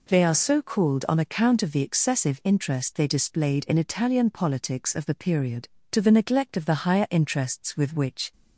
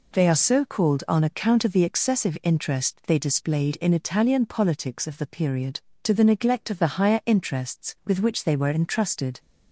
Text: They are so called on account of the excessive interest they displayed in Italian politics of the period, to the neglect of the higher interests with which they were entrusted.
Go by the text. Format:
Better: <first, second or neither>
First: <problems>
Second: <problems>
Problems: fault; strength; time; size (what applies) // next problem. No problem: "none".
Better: second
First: stops before "they were entrusted"; at 8.3 s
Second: none